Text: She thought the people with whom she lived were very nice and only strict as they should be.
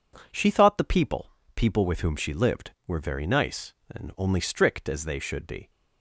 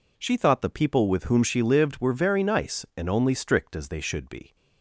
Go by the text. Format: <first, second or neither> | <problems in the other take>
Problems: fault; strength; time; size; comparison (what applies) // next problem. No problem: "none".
second | says "people" twice; at 1.5 s